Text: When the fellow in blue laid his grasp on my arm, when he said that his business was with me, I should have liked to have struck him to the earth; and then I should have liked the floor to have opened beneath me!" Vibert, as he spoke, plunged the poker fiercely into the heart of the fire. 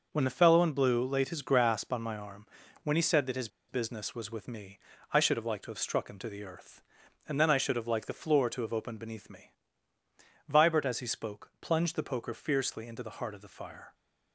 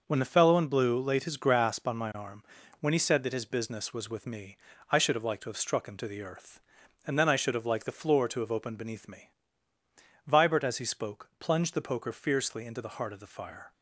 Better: second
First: pauses between "his" and "business"; slight; at 3.4 s; 0.21 s long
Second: none

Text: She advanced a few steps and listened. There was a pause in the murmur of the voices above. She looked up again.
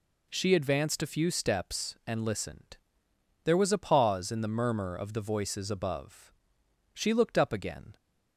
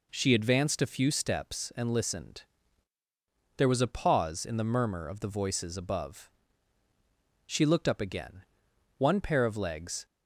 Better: first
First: none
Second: goes on to say "One pair of legs"; noticeable; from 8.9 s on; 1.0 s long

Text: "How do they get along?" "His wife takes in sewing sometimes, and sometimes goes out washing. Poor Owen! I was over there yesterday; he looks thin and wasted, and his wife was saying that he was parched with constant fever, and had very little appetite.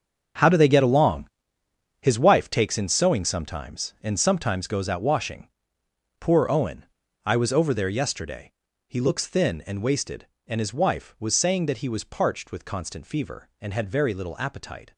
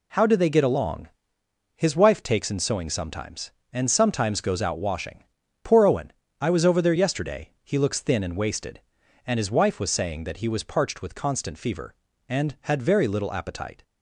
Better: second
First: gets quieter; strong; throughout; 12 dB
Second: none

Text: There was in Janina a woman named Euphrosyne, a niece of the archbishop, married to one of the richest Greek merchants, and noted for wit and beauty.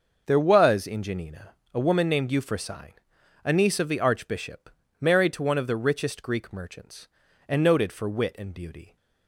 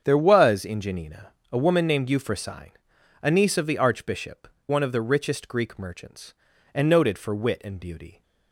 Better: first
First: pauses between "Janina" and "a"; slight; at 1.5 s; 0.18 s long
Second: starts louder than the rest; strong; until 1.0 s; 7.5 dB // pauses between "Janina" and "a"; slight; at 1.3 s; 0.18 s long // skips "married to"; at 4.5 s

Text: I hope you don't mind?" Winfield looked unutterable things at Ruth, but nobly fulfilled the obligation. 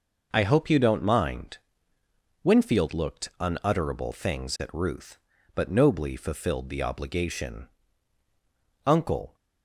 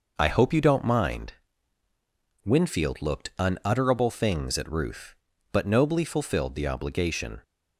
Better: second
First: goes on to say "Uncle"; from 8.8 s on; 0.50 s long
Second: none

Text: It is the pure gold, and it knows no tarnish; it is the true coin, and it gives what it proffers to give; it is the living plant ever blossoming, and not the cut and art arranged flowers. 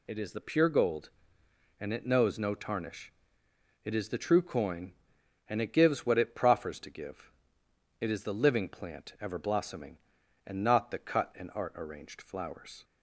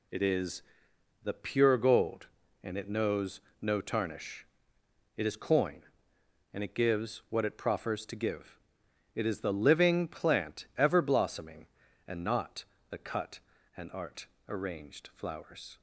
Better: first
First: none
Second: pauses between "is" and "the"; noticeable; at 0.6 s; 0.62 s long // pauses between "knows" and "no"; slight; at 3.3 s; 0.20 s long // skips "the true"; at 5.3 s // pauses between "not" and "the"; slight; at 12.6 s; 0.24 s long // pauses between "art" and "arranged"; slight; at 14.2 s; 0.20 s long

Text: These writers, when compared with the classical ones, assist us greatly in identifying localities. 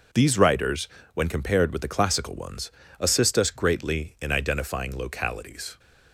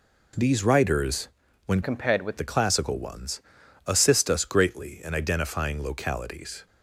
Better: first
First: none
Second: changes voice from "compared" to "with"; from 1.8 to 2.3 s; 0.5 s long

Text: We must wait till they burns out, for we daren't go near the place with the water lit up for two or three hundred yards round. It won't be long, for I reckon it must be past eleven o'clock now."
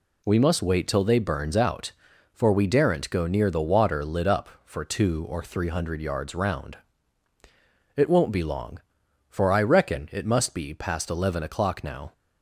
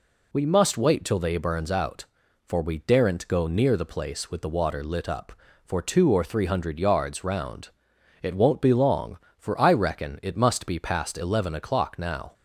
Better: second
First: skips "the place with"; at 3.4 s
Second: none

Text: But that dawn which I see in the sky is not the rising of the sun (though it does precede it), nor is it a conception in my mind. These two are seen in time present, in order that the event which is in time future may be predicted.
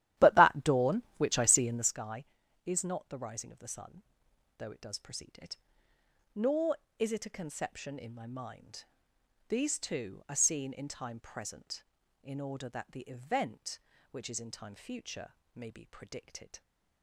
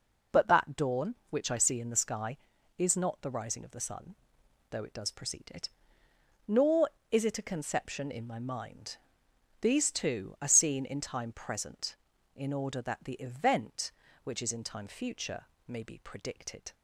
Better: second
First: starts louder than the rest; strong; until 2.0 s; 13 dB // pauses between "future" and "may"; slight; at 15.3 s; 0.20 s long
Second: pauses between "future" and "may"; slight; at 15.4 s; 0.20 s long

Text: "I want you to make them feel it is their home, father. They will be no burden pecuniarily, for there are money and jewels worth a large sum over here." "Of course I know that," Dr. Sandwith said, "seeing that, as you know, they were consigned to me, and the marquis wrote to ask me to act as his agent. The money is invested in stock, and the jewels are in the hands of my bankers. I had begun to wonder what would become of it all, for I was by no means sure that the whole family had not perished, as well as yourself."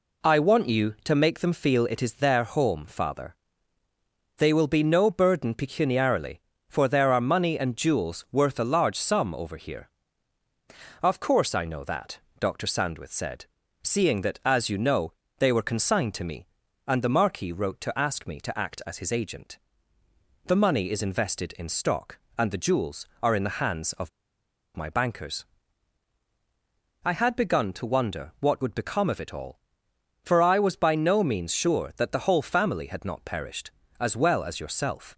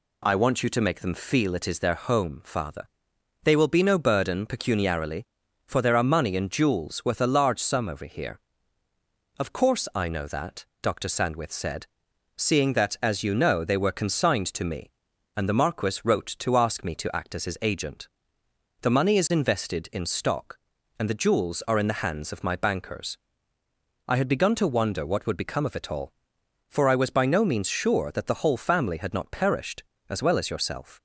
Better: second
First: pauses between "of" and "my"; noticeable; at 24.0 s; 0.67 s long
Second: none

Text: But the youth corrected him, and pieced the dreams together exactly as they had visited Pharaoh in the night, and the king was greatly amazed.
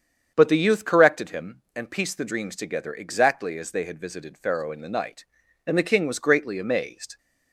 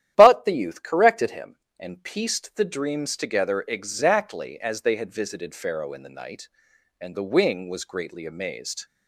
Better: first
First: starts louder than the rest; strong; until 1.3 s; 7.5 dB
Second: starts louder than the rest; strong; until 1.1 s; 11.5 dB // says "wing" for "king"; at 7.2 s

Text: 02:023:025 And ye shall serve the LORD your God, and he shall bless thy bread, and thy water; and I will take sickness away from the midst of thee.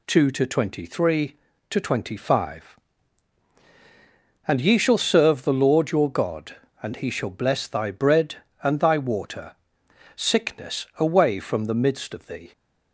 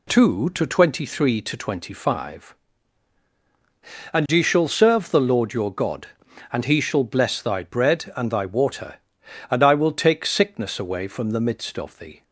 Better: second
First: skips "and I will take"; at 9.8 s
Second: none

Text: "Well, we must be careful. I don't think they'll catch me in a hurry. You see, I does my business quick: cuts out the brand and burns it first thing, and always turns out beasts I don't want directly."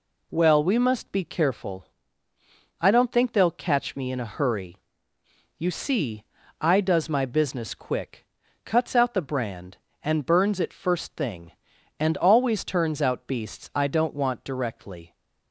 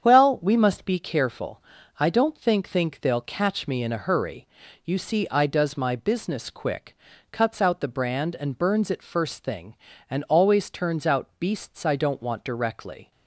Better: first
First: none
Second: starts louder than the rest; strong; until 1.0 s; 8 dB // says "think" twice; at 2.6 s

